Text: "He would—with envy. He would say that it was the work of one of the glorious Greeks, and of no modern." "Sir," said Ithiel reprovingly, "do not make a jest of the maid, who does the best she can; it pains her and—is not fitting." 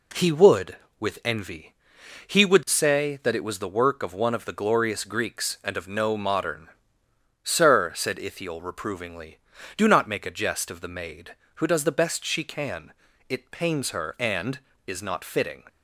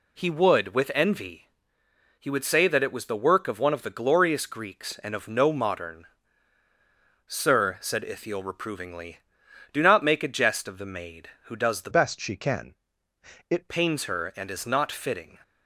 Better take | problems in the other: first | changes voice from "best" to "it"; from 11.8 to 13.6 s; 1.8 s long

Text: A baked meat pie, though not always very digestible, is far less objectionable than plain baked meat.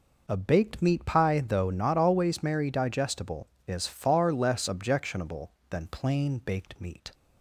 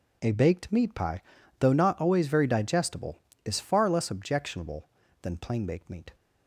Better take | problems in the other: second | says "merry" for "very"; at 2.4 s

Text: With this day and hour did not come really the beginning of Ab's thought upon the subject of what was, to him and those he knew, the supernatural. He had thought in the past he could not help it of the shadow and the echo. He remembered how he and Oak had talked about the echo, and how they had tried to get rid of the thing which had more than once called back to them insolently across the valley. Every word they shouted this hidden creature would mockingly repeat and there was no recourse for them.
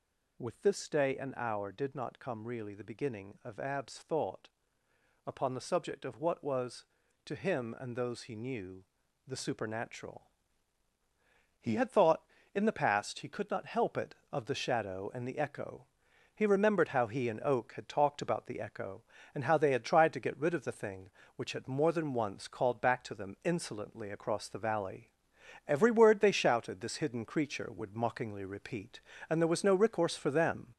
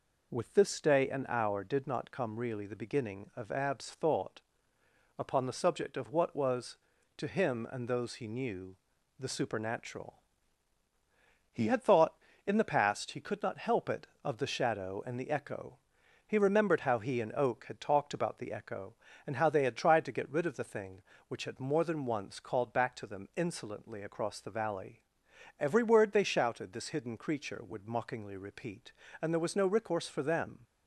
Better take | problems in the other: second | gets louder; noticeable; throughout; 4.5 dB // pauses between "thought" and "upon"; noticeable; at 4.4 s; 0.78 s long; noticeable in the second

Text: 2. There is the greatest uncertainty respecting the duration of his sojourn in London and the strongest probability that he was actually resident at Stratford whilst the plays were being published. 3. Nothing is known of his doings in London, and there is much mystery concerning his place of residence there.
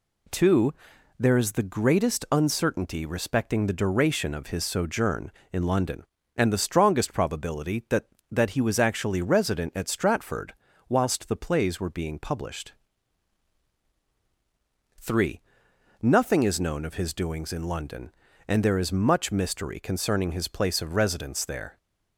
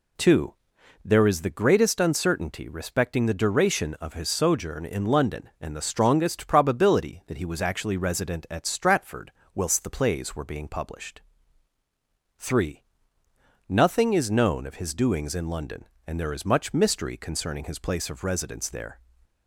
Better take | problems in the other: second | says "that" twice; at 8.2 s // pauses between "Stratford" and "whilst"; slight; at 10.5 s; 0.34 s long; slight in the second

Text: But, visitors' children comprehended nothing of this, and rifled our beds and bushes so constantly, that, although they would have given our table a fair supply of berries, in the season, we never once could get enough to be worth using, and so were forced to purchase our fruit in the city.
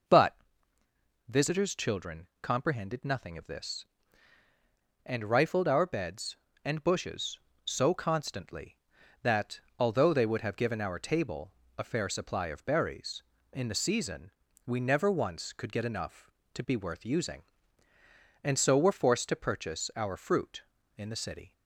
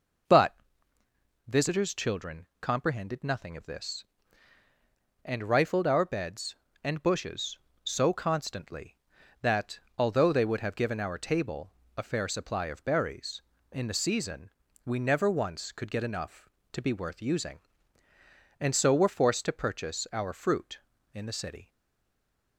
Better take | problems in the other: first | pauses between "table" and "a"; slight; at 11.6 s; 0.26 s long; slight in the first // stays silent after the last word; slight; from 21.6 s on; 0.9 s long

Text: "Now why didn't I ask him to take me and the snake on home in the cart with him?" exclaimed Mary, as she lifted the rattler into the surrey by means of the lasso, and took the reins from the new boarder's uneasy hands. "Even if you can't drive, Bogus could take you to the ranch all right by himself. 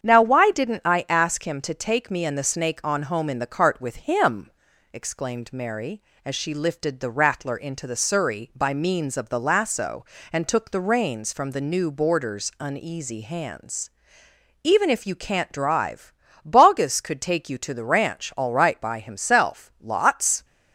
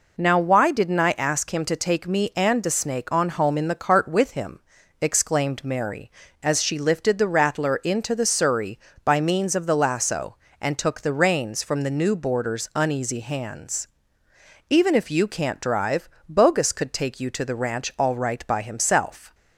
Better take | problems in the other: second | starts louder than the rest; strong; until 1.0 s; 8 dB // goes on to say "Lots"; noticeable; from 19.8 s on; 0.64 s long

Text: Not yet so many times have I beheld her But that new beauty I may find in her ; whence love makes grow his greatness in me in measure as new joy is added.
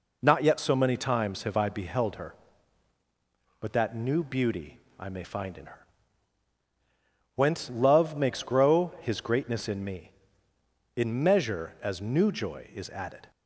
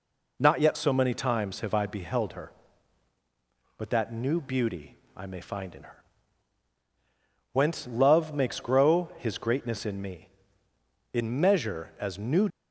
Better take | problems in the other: first | pauses between "beauty" and "I"; slight; at 4.9 s; 0.20 s long; slight in the first // stops before "joy is added"; at 12.4 s

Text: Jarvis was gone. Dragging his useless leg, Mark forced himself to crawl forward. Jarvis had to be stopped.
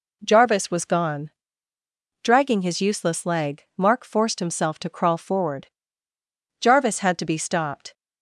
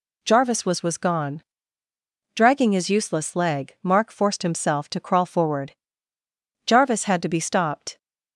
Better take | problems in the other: first | says "was" twice; at 0.8 s

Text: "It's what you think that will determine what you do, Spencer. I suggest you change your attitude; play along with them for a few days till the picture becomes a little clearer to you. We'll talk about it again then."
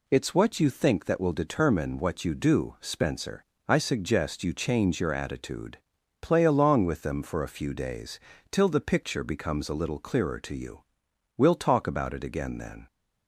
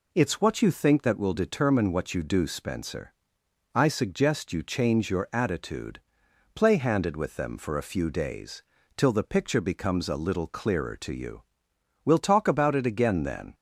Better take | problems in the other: first | says "handed" for "along"; at 6.7 s // pauses between "days" and "till"; slight; at 8.6 s; 0.34 s long; slight in the first

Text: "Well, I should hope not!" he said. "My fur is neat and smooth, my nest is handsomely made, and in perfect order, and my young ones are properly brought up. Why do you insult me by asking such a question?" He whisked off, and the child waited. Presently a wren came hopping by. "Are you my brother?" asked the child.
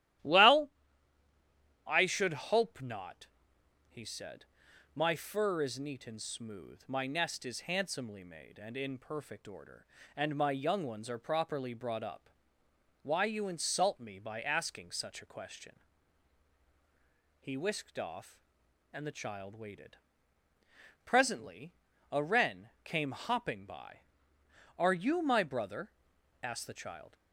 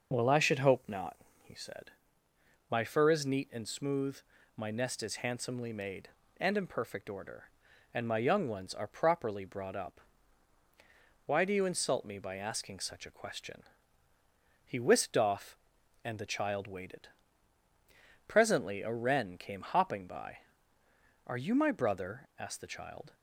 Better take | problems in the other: second | starts louder than the rest; strong; until 2.3 s; 13.5 dB // skips "do"; at 13.2 s // pauses between "Presently" and "a"; at 21.7 s; 0.40 s long

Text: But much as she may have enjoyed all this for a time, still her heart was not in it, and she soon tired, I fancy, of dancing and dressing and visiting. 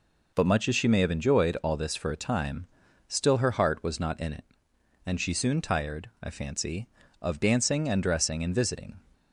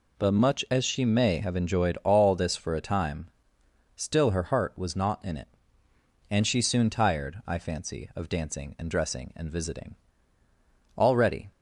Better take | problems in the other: first | goes on to say "Already"; from 10.9 s on; 0.54 s long

